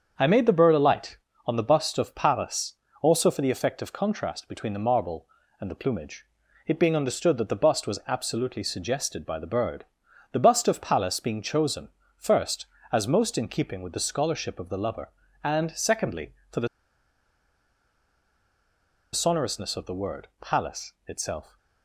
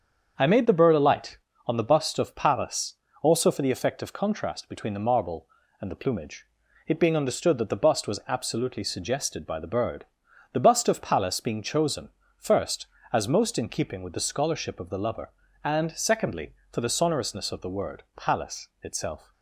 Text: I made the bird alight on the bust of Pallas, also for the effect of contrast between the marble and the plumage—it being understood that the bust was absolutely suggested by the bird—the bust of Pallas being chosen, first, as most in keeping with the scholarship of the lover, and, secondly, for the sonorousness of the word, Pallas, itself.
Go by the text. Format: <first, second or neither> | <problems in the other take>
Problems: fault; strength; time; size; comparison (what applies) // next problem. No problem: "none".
second | starts louder than the rest; until 1.1 s; 7 dB; also in the second // pauses between "the" and "sonorousness"; strong; at 16.6 s; 2.4 s long